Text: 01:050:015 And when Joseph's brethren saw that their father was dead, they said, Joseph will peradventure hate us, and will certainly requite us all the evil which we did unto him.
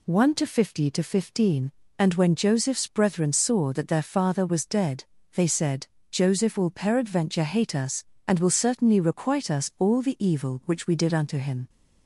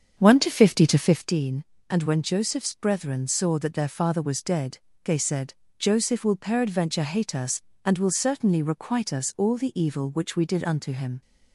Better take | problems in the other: first | starts louder than the rest; strong; until 1.4 s; 7 dB

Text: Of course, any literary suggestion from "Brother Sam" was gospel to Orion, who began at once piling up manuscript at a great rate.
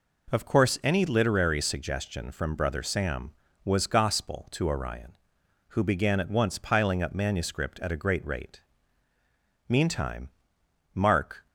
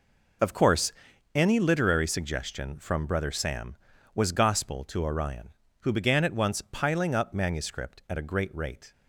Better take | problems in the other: second | goes on to say "Meantime Mark"; strong; from 9.6 s on; 1.7 s long

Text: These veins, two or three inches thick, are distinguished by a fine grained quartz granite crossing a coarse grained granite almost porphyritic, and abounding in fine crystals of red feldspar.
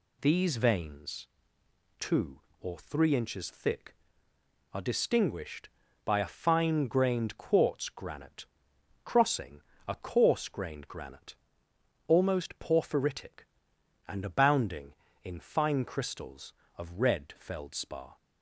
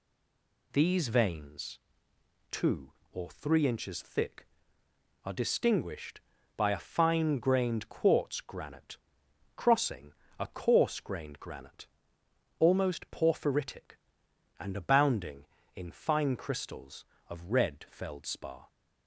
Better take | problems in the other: first | stays silent before the first word; slight; until 0.7 s; 0.7 s long // pauses between "granite" and "crossing"; noticeable; at 8.9 s; 0.60 s long; noticeable in the first // pauses between "crossing" and "a"; slight; at 10.1 s; 0.26 s long; slight in the first // pauses between "granite" and "almost"; noticeable; at 11.8 s; 0.74 s long; noticeable in the first

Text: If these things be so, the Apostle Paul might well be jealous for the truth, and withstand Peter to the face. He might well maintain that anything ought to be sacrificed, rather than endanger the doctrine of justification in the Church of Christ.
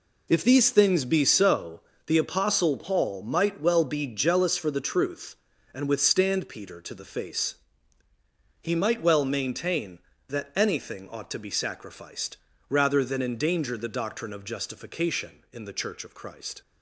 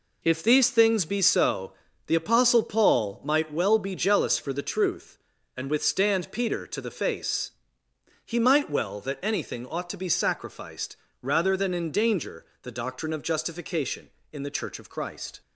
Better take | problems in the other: first | skips "maintain"; at 9.0 s // pauses between "endanger" and "the"; slight; at 12.4 s; 0.18 s long

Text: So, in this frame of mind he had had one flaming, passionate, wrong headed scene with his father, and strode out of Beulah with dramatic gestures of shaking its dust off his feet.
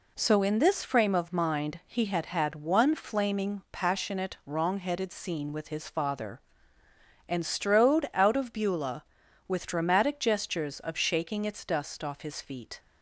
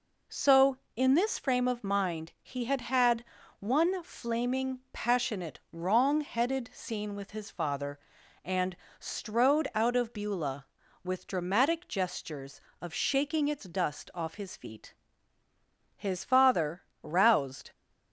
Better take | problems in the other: first | pauses between "had" and "one"; at 3.2 s; 0.38 s long // pauses between "and" and "strode"; slight; at 8.7 s; 0.24 s long // goes on to say "His father roused"; strong; from 15.9 s on; 1.7 s long

